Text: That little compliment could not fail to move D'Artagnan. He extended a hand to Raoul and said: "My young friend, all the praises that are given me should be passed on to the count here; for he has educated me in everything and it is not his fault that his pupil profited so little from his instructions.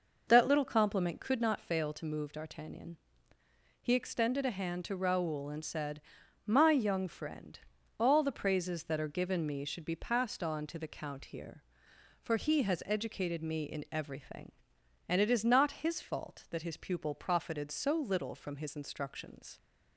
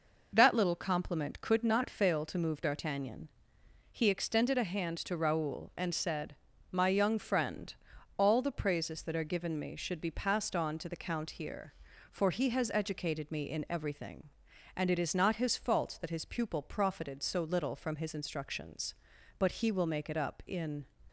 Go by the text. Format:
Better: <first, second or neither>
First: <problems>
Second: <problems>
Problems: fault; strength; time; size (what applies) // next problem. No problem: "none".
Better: first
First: none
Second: goes on to say "But he will make it up in"; from 19.3 s on; 1.4 s long